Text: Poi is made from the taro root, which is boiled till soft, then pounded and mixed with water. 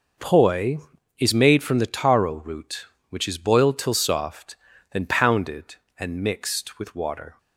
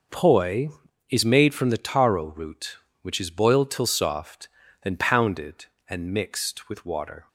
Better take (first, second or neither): neither